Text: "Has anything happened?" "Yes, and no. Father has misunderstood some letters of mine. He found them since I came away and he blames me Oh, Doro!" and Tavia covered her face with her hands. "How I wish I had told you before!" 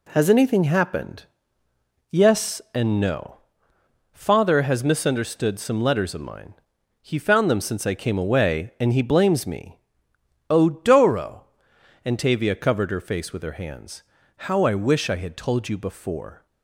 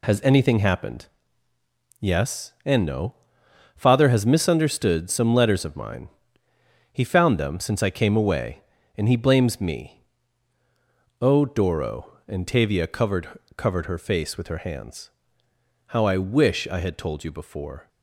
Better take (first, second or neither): first